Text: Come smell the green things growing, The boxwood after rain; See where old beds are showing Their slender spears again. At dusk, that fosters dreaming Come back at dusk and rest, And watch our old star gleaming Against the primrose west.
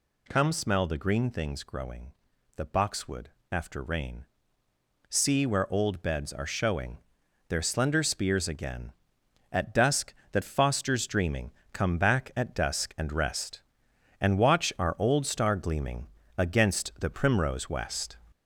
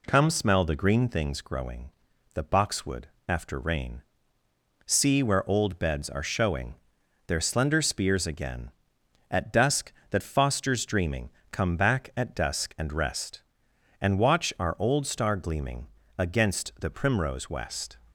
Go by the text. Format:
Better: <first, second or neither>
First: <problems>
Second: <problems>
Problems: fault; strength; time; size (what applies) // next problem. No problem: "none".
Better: second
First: gets louder; noticeable; throughout; 4.5 dB // pauses between "boxwood" and "after"; slight; at 3.2 s; 0.22 s long // pauses between "showing" and "Their"; noticeable; at 6.9 s; 0.52 s long // pauses between "dreaming" and "Come"; slight; at 11.5 s; 0.22 s long // pauses between "gleaming" and "Against"; slight; at 16.0 s; 0.32 s long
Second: pauses between "boxwood" and "after"; slight; at 3.0 s; 0.20 s long // pauses between "showing" and "Their"; noticeable; at 6.7 s; 0.54 s long // pauses between "dreaming" and "Come"; slight; at 11.2 s; 0.22 s long // pauses between "gleaming" and "Against"; slight; at 15.8 s; 0.32 s long